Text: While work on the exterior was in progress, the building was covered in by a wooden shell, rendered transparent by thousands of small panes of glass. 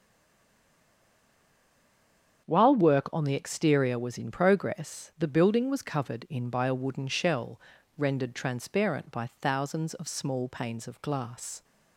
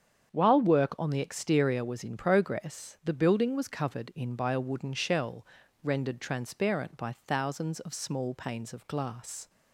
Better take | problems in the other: second | stays silent before the first word; until 2.4 s; 2.4 s long // starts louder than the rest; strong; until 3.5 s; 8 dB; strong in the second

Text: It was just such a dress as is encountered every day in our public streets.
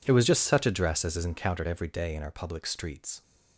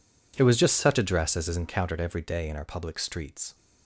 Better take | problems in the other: neither | none

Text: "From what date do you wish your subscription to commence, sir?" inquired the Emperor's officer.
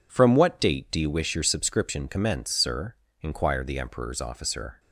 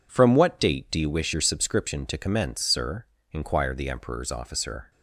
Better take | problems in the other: second | skips "to"; at 2.0 s

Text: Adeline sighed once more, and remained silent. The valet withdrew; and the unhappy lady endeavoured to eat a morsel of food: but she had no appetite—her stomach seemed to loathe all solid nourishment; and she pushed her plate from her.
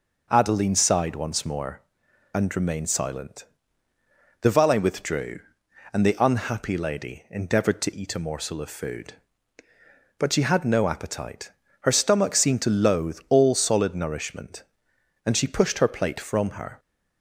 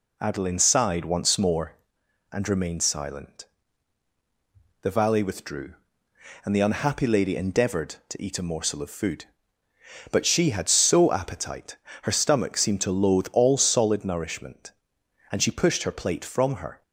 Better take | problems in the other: first | says "so" for "no"; at 10.6 s

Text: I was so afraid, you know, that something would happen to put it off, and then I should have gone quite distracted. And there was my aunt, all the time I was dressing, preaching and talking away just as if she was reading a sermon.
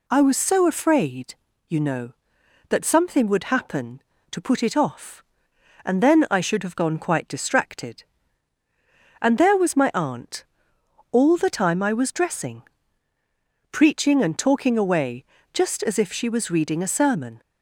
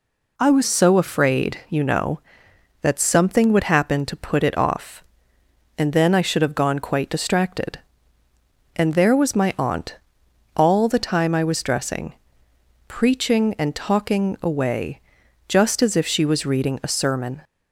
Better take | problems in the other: first | changes voice at "so"; from 0.6 s on; 16.8 s long // pauses between "away" and "just"; noticeable; at 15.0 s; 0.48 s long; slight in the first

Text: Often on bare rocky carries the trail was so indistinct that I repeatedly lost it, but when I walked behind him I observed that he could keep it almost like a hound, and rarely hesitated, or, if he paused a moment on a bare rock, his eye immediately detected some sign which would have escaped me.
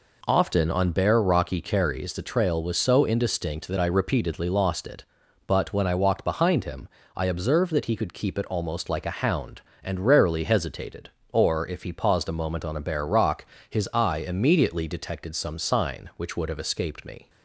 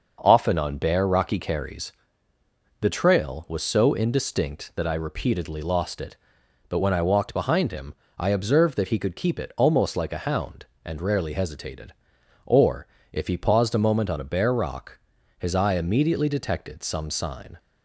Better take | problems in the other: first | starts louder than the rest; noticeable; until 1.2 s; 6 dB // pauses between "carries" and "the"; noticeable; at 1.9 s; 0.90 s long // pauses between "him" and "I"; slight; at 7.9 s; 0.24 s long; slight in the first // stops before "which would have escaped me"; at 17.5 s

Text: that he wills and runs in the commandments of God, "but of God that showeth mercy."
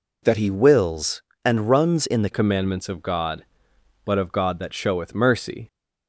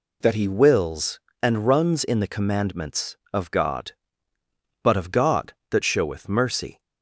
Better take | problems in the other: second | changes voice at "commandments"; from 2.3 s on; 3.3 s long

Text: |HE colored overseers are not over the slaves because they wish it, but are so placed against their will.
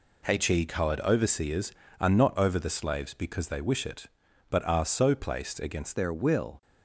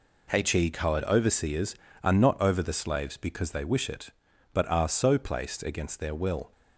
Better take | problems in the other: second | changes voice at "their"; from 5.9 s on; 0.7 s long

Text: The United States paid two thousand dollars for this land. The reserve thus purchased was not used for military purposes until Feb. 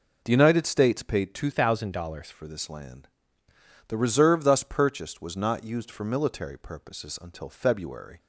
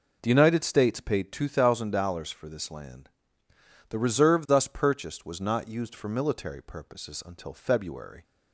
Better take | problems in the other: second | changes voice from "thousand" to "dollars"; from 1.5 to 2.3 s; 0.8 s long

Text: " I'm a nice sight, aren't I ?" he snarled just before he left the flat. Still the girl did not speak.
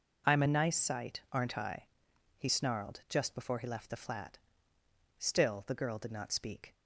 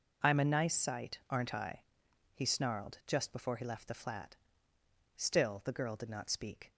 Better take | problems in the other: neither | none

